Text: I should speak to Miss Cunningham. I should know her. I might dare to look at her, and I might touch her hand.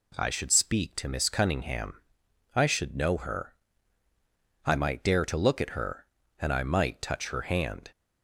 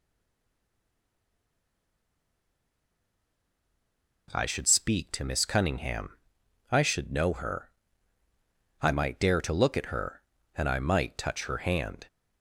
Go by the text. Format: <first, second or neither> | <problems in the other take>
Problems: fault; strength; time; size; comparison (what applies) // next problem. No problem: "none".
first | stays silent before the first word; strong; until 4.2 s; 4.2 s long